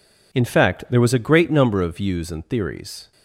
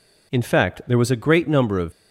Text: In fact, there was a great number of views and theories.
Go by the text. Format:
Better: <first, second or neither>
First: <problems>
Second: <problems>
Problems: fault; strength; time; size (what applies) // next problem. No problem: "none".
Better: first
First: none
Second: stops before "views and theories"; at 1.9 s